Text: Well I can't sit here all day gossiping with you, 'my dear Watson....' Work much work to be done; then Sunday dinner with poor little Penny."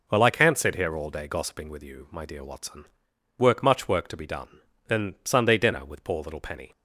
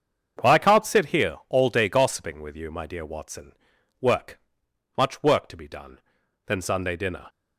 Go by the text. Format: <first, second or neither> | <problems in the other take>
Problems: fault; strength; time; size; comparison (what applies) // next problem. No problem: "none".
first | starts louder than the rest; until 1.5 s; 7 dB // pauses between "Work" and "much"; noticeable; at 4.3 s; 0.60 s long // stops before "with poor little Penny"; at 7.2 s